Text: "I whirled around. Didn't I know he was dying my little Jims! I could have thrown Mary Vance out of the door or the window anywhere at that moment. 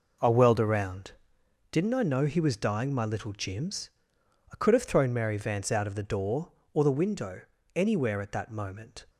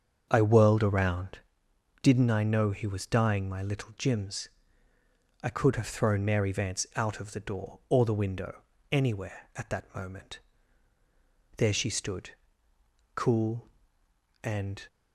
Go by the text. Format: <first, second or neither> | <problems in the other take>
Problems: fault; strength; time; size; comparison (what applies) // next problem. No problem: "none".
first | starts louder than the rest; strong; until 1.3 s; 7.5 dB // pauses between "window" and "anywhere"; slight; at 8.6 s; 0.32 s long; slight in the first // goes on to say "There she stood cool and"; strong; from 11.5 s on; 3.3 s long